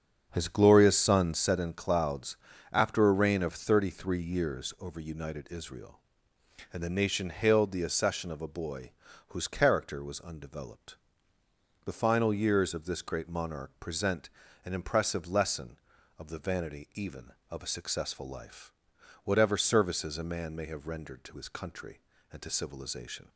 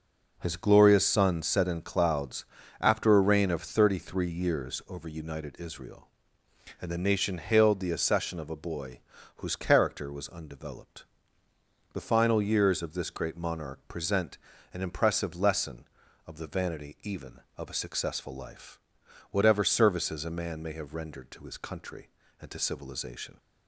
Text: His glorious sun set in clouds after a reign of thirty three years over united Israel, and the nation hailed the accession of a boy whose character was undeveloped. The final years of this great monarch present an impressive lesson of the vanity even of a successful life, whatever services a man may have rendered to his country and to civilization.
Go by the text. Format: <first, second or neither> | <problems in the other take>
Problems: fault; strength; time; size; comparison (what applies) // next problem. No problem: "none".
second | starts louder than the rest; until 1.5 s; 7 dB // pauses between "clouds" and "after"; slight; at 2.3 s; 0.34 s long; slight in the second // pauses between "boy" and "whose"; slight; at 8.9 s; 0.36 s long; slight in the second // pauses between "present" and "an"; slight; at 14.2 s; 0.36 s long; slight in the second